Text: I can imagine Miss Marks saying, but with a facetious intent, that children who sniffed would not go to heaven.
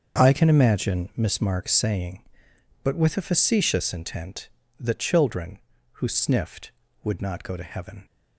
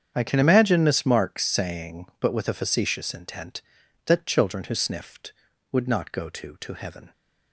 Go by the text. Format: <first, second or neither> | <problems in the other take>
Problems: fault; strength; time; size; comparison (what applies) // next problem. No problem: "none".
first | starts louder than the rest; strong; until 1.1 s; 8 dB; also in the first // says "to" twice; at 6.5 s